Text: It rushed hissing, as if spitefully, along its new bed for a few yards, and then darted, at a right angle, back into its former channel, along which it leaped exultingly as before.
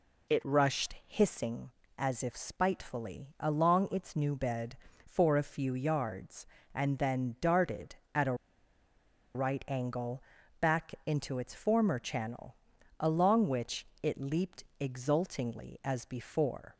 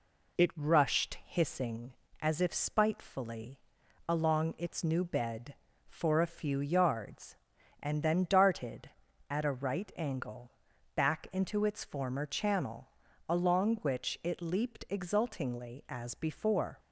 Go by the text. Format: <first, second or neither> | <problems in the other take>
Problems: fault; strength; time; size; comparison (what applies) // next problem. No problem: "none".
second | pauses between "a" and "right"; at 8.3 s; 1.0 s long // pauses between "which" and "it"; slight; at 13.8 s; 0.16 s long // pauses between "leaped" and "exultingly"; slight; at 14.6 s; 0.18 s long